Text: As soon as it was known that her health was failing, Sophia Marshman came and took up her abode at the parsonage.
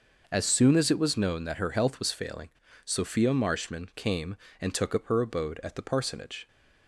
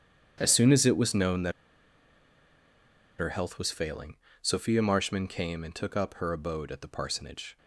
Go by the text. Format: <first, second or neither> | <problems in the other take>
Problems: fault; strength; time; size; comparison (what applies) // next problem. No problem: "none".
first | starts louder than the rest; strong; until 1.3 s; 8.5 dB // pauses between "that" and "her"; strong; at 1.5 s; 1.6 s long